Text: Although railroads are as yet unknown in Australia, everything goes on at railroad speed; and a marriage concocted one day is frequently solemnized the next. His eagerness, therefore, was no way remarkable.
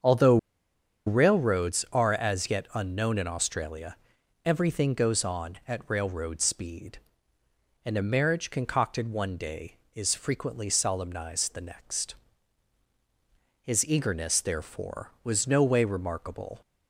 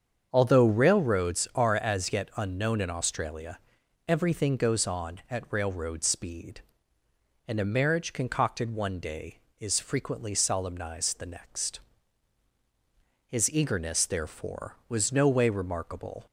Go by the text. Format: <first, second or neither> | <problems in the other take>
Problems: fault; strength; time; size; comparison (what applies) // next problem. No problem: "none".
second | starts louder than the rest; strong; until 1.7 s; 7 dB; strong in the second // pauses between "Although" and "railroads"; noticeable; at 0.3 s; 0.69 s long